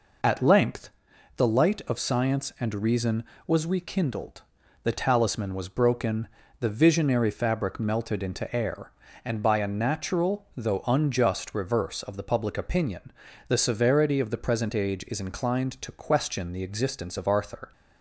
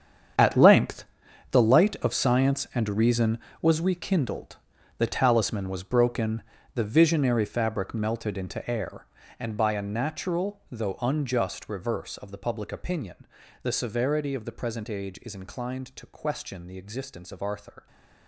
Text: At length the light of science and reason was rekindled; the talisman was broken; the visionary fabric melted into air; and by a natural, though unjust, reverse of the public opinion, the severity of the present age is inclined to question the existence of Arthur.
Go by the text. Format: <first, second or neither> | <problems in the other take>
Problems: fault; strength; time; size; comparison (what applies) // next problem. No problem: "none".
first | gets quieter; strong; throughout; 14.5 dB // pauses between "length" and "the"; noticeable; at 1.0 s; 0.48 s long; noticeable in the first